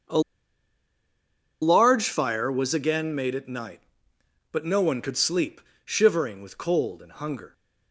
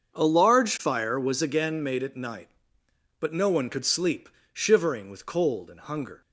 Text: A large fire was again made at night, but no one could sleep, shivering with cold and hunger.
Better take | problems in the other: second | starts louder than the rest; until 2.5 s; 6.5 dB; also in the second // pauses between "A" and "large"; strong; at 0.1 s; 1.4 s long

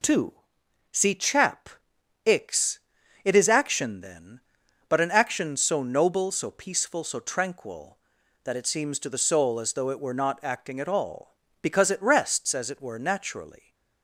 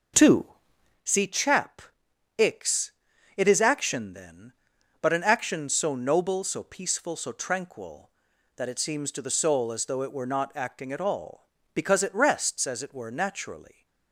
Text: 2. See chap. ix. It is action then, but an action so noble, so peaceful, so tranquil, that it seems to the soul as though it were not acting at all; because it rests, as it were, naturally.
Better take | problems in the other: first | starts louder than the rest; until 1.0 s; 6 dB

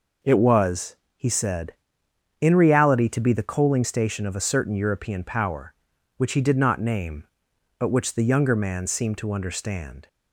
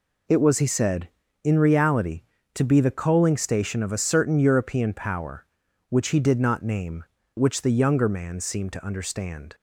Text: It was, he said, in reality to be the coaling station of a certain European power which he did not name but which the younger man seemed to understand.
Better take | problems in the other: first | skips "but"; at 7.2 s

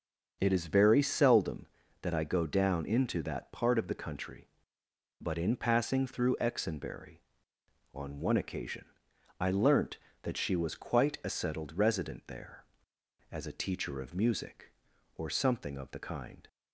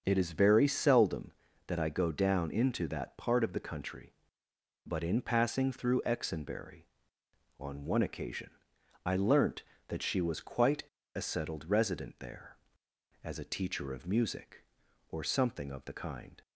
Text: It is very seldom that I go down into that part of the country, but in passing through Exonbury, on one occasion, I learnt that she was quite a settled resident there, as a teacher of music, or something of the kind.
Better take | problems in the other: first | starts louder than the rest; until 1.0 s; 6 dB; also in the first // pauses between "quite" and "a"; slight; at 10.8 s; 0.31 s long

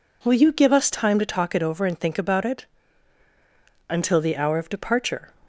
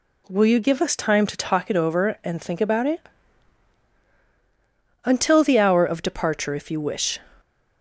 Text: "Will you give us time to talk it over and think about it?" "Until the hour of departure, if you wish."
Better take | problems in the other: second | stops before "if you wish"; at 5.4 s

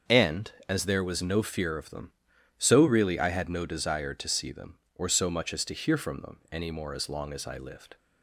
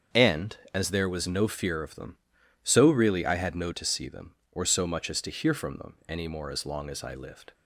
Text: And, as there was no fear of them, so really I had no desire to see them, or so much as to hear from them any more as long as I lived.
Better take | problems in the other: first | starts louder than the rest; until 1.3 s; 7 dB; also in the first // skips "desire"; at 3.7 s

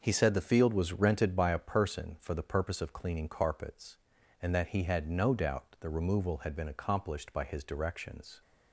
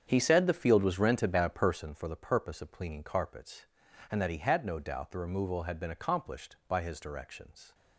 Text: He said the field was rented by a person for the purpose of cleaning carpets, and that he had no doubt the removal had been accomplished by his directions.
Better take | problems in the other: first | starts louder than the rest; strong; until 1.9 s; 7.5 dB

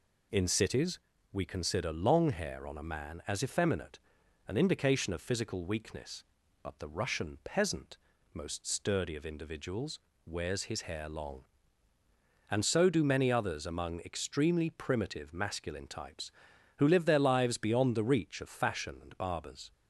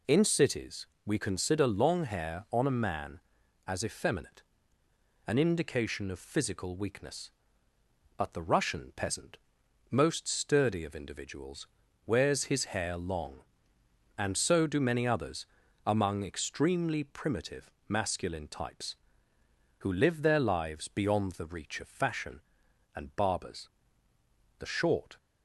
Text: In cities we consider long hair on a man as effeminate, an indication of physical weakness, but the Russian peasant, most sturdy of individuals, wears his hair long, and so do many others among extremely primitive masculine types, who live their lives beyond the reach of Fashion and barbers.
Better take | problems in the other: first | pauses between "cities" and "we"; slight; at 0.8 s; 0.22 s long; slight in the first // pauses between "others" and "among"; at 15.4 s; 0.40 s long // pauses between "primitive" and "masculine"; slight; at 17.7 s; 0.18 s long // goes on to say "The short"; from 24.5 s on; 0.58 s long

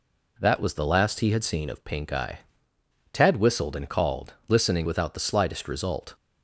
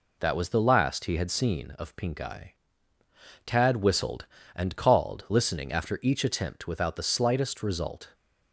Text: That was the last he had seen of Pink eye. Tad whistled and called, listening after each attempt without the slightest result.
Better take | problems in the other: second | skips "after each attempt"; at 4.8 s

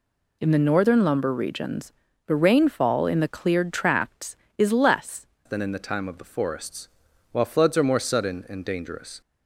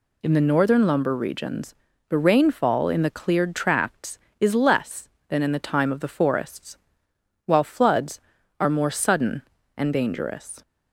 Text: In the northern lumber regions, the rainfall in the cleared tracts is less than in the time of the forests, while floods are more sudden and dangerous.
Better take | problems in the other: second | changes voice at "than"; from 5.4 s on; 3.8 s long

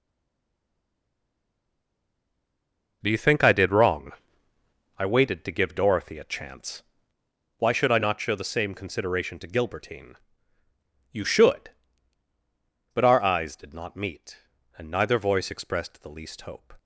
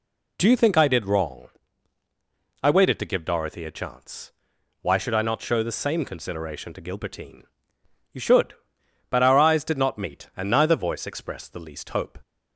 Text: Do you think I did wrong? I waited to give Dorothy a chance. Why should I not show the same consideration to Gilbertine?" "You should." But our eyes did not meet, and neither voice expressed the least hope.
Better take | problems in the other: second | stays silent before the first word; strong; until 3.0 s; 3.0 s long

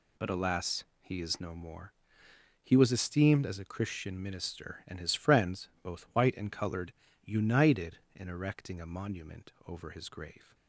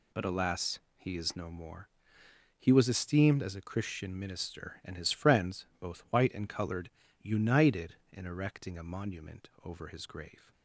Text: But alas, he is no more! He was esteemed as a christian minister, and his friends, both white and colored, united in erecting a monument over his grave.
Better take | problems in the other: neither | pauses between "monument" and "over"; slight; the same in both

